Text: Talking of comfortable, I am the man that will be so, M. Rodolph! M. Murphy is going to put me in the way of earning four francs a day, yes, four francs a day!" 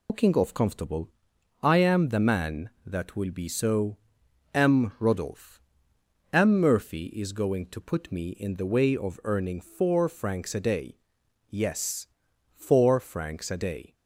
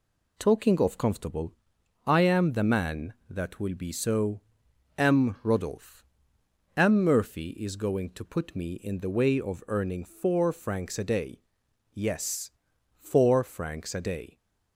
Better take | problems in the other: second | loses the start of "Talking"; at 0.0 s; 150 ms

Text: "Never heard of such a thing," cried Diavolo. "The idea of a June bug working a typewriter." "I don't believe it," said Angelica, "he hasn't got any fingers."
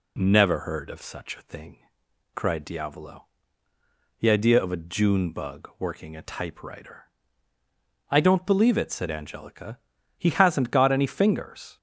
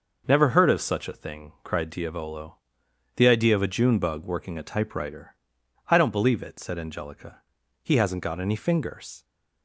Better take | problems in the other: neither | none

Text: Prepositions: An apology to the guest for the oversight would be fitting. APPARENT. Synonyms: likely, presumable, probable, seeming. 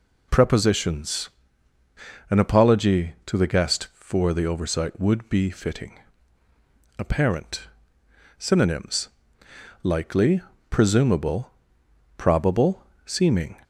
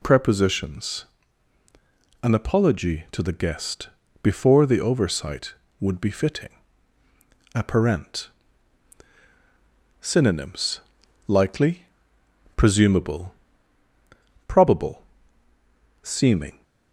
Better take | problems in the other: first | says "before" for "for"; at 4.2 s

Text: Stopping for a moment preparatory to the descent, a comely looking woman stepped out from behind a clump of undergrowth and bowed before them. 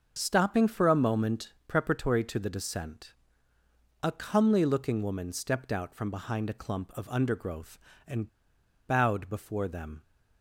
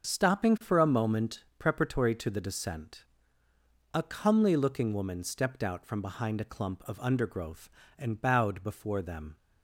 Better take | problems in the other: second | starts louder than the rest; until 1.1 s; 6.5 dB; also in the second // pauses between "and" and "bowed"; noticeable; at 8.2 s; 0.59 s long

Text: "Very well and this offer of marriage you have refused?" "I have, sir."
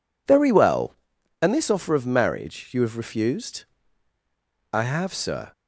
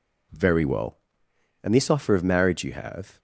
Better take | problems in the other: first | stops before "refused I have sir"; at 3.1 s

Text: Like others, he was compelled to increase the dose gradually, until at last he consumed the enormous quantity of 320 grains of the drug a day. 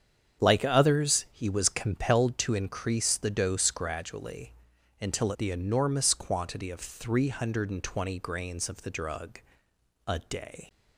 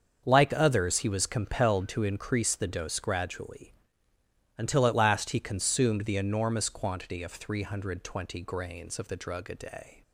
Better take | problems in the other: second | starts louder than the rest; strong; until 1.4 s; 8 dB; also in the second // skips "at last he consumed"; at 5.3 s // pauses between "drug" and "a"; noticeable; at 9.3 s; 0.66 s long

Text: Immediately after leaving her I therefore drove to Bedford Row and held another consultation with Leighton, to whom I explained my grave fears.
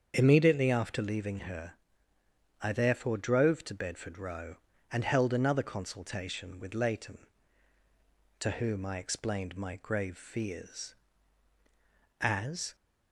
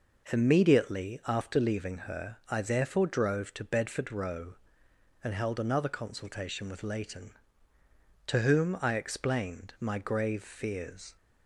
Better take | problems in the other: second | starts louder than the rest; strong; until 1.1 s; 7 dB // pauses between "her" and "I"; noticeable; at 1.7 s; 0.88 s long // goes on to say "As"; from 12.2 s on; 0.54 s long

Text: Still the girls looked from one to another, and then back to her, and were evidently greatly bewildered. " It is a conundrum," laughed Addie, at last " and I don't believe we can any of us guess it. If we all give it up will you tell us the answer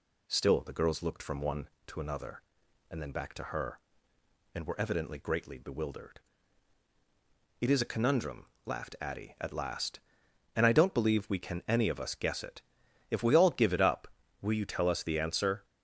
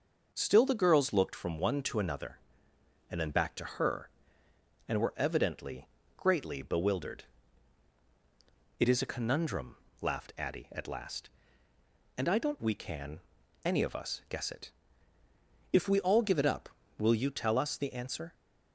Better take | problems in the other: first | starts louder than the rest; until 1.3 s; 6.5 dB // pauses between "evidently" and "greatly"; slight; at 5.8 s; 0.30 s long // skips "believe"; at 12.6 s // pauses between "can" and "any"; at 13.1 s; 0.44 s long

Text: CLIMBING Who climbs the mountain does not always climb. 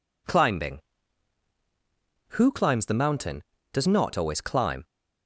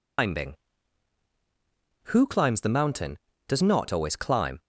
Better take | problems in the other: first | loses the start of "CLIMBING"; at 0.1 s; 170 ms

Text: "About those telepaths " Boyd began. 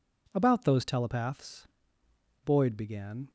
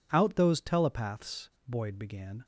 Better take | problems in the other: first | says "Out" for "About"; at 0.1 s

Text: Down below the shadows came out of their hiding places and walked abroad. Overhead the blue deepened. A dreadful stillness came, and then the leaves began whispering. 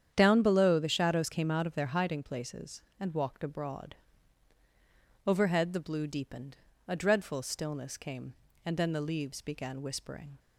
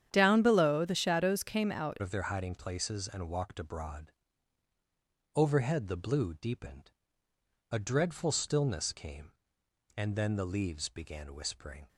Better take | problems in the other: first | starts louder than the rest; strong; until 1.1 s; 9.5 dB; strong in the first // changes voice at "of"; from 2.0 s on; 9.8 s long

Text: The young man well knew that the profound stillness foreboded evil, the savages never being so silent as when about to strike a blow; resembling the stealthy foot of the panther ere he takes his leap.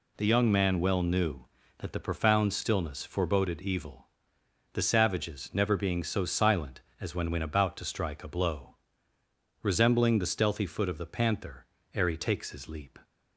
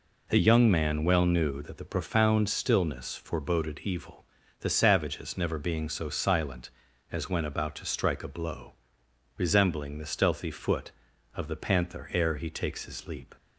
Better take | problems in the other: second | says "when" twice; at 7.3 s // pauses between "panther" and "ere"; slight; at 11.6 s; 0.30 s long

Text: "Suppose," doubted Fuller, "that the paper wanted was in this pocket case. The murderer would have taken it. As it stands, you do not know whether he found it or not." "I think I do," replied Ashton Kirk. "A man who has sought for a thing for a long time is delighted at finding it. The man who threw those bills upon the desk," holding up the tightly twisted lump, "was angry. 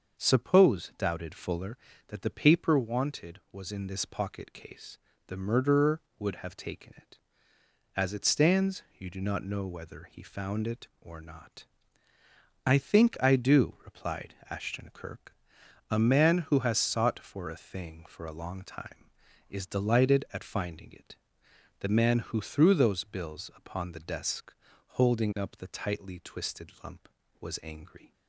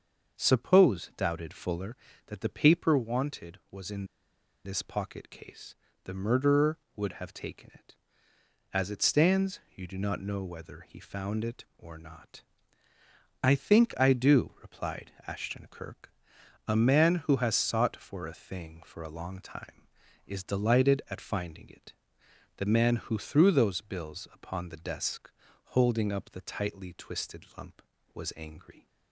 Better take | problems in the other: first | starts louder than the rest; until 1.4 s; 6.5 dB; also in the first // pauses between "in" and "this"; noticeable; at 4.0 s; 0.60 s long // pauses between "replied" and "Ashton"; slight; at 15.1 s; 0.16 s long; slight in the first

